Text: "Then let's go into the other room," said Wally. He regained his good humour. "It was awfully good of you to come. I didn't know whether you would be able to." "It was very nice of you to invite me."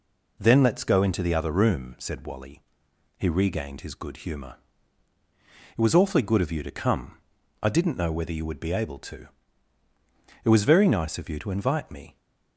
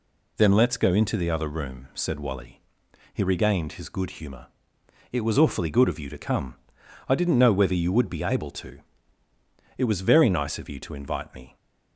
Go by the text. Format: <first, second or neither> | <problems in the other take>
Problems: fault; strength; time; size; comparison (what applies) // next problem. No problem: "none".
neither | none